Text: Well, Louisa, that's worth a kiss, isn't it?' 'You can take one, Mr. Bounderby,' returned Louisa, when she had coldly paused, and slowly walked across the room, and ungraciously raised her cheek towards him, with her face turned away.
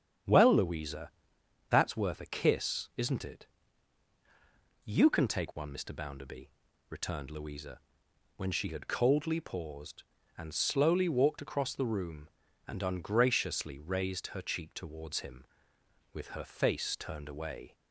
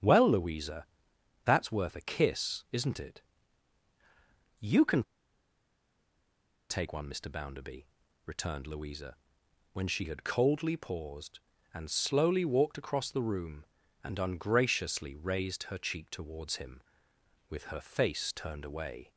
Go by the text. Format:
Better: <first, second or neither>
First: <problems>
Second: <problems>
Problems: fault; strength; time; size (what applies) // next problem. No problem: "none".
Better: first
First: starts louder than the rest; strong; until 1.9 s; 8.5 dB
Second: starts louder than the rest; strong; until 1.6 s; 8.5 dB // pauses between "can" and "take"; strong; at 5.0 s; 1.6 s long